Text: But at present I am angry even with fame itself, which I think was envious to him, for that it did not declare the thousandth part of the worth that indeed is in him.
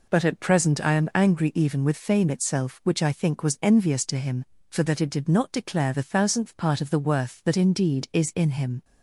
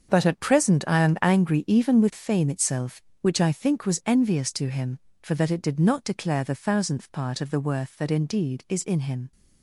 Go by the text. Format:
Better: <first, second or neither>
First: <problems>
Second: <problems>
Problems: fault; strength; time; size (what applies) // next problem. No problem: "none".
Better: first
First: none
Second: gets quieter; strong; throughout; 11.5 dB